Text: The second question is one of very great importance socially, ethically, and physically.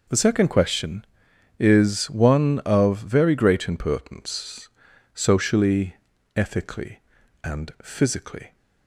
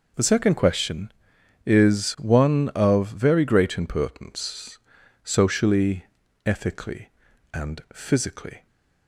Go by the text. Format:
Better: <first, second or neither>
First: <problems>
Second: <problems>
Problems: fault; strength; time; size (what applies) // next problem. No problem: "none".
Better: neither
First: pauses between "importance" and "socially"; at 4.6 s; 0.44 s long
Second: pauses between "importance" and "socially"; at 4.7 s; 0.44 s long